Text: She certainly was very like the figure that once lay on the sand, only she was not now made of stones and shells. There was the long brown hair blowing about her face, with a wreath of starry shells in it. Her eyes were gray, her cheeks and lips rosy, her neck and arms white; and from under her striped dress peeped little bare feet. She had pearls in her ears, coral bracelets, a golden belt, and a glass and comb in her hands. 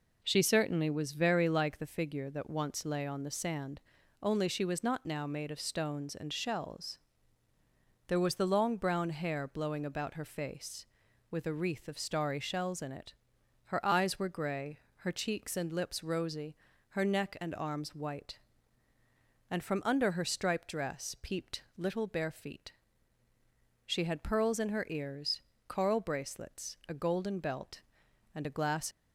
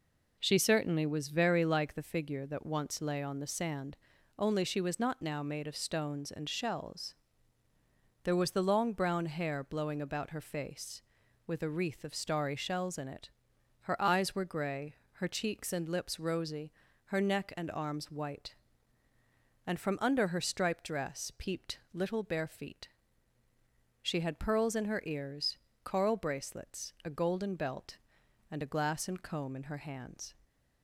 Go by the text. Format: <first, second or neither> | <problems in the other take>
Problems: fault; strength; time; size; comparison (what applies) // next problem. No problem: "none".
second | stops before "and comb in her hands"; at 28.9 s